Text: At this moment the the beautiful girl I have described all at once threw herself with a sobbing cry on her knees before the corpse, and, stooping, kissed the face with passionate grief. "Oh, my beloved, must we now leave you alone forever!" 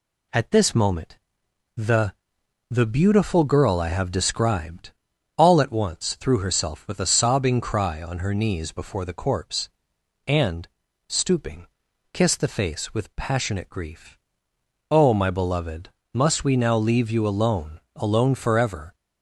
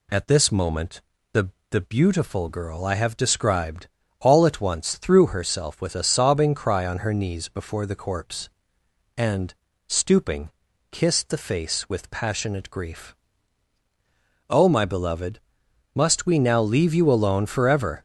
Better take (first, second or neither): second